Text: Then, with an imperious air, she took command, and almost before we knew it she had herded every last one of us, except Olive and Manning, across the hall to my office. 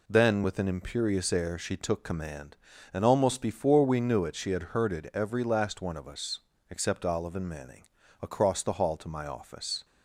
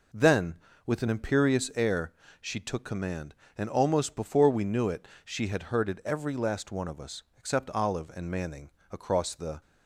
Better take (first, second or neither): first